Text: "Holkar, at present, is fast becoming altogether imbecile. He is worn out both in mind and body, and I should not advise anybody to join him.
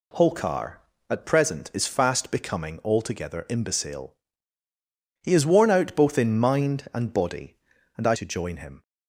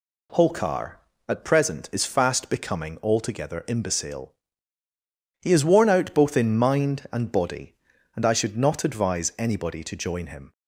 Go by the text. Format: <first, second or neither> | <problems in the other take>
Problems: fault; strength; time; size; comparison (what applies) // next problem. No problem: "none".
second | skips "should not advise anybody"; at 8.1 s